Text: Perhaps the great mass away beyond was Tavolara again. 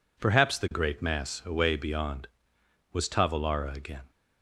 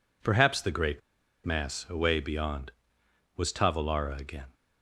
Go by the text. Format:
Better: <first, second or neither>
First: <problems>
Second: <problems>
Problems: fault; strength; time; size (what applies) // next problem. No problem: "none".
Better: first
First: none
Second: pauses between "great" and "mass"; at 1.0 s; 0.43 s long